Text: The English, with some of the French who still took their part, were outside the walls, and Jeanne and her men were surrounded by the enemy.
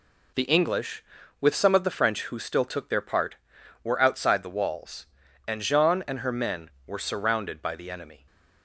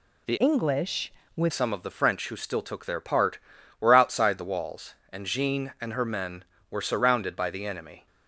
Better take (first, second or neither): first